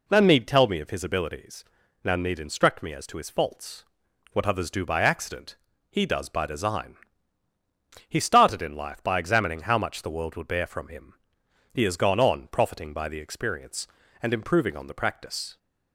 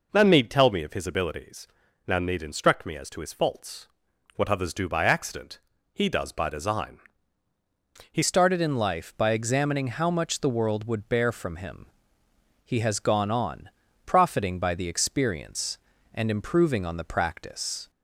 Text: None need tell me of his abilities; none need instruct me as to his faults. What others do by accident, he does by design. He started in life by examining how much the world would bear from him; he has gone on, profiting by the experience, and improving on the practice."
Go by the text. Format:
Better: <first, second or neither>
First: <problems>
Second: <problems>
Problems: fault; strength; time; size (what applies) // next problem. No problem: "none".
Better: first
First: none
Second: changes voice at "started"; from 8.2 s on; 9.6 s long